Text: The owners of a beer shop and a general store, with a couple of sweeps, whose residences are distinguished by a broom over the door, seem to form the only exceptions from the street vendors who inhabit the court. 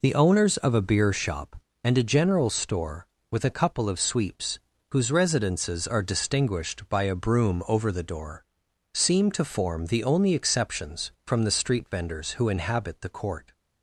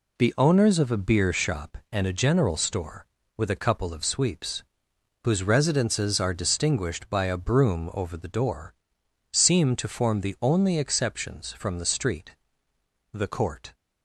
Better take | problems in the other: first | skips "vendors who inhabit"; at 12.7 s

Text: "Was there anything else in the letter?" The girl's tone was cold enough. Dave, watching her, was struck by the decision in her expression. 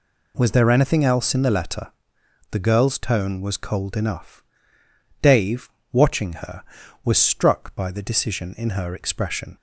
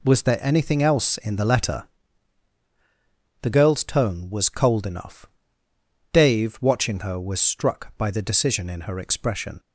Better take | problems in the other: neither | none

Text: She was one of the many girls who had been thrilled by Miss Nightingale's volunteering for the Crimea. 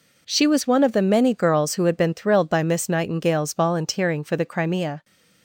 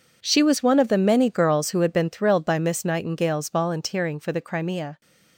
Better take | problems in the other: first | gets quieter; strong; throughout; 15.5 dB

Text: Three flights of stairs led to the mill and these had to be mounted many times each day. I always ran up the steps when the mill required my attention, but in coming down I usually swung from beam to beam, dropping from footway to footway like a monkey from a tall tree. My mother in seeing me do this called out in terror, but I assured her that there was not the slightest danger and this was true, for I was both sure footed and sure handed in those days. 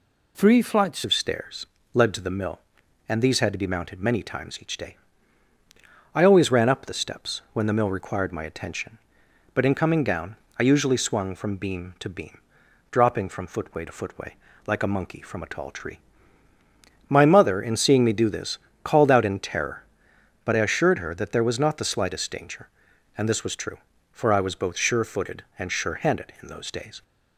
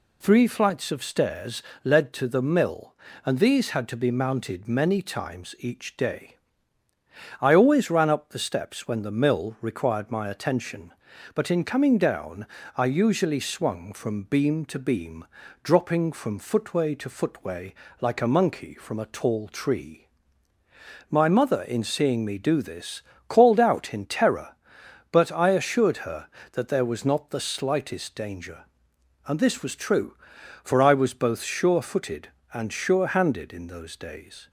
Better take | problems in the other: second | changes voice at "of"; from 1.0 s on; 26.0 s long // pauses between "stairs" and "led"; slight; at 1.6 s; 0.26 s long; slight in the second // pauses between "down" and "I"; slight; at 10.3 s; 0.22 s long; slight in the second // pauses between "footway" and "like"; slight; at 14.3 s; 0.30 s long; slight in the second // pauses between "this" and "called"; slight; at 18.5 s; 0.28 s long; slight in the second

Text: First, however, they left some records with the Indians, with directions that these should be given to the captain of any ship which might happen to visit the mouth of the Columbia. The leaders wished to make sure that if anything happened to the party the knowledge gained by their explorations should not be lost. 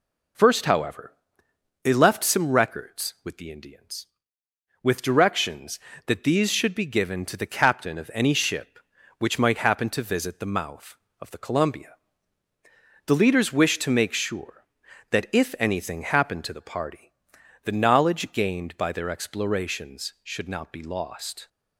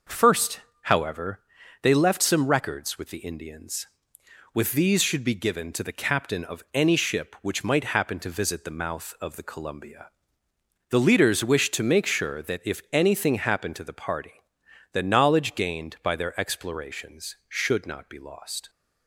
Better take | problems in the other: first | skips "directions that"; at 4.7 s // pauses between "party" and "the"; noticeable; at 14.3 s; 0.62 s long; noticeable in the first

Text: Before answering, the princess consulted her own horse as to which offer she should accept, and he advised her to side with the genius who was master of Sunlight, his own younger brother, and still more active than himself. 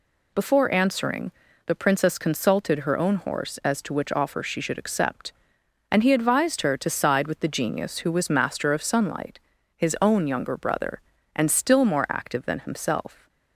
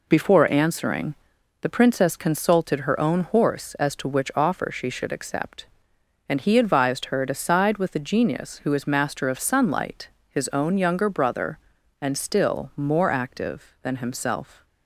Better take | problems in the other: first | says "is" for "was"; at 8.7 s

